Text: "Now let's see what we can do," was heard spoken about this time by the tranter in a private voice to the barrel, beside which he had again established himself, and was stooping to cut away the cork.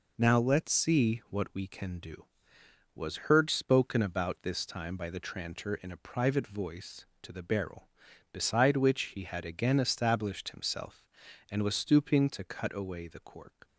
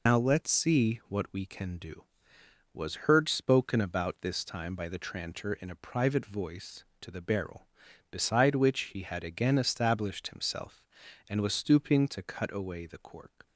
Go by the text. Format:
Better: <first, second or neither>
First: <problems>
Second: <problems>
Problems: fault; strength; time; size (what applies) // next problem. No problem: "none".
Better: first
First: none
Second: loses the start of "Now"; at 0.0 s; 100 ms